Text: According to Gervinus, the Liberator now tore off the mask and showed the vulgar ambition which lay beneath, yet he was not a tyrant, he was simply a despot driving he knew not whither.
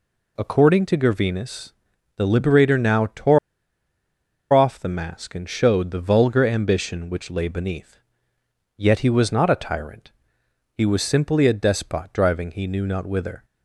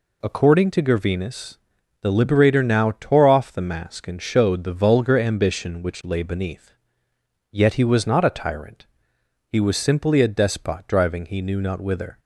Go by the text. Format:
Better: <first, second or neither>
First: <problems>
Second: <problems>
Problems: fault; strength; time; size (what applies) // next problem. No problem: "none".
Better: second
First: pauses between "tore" and "off"; at 3.3 s; 1.1 s long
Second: none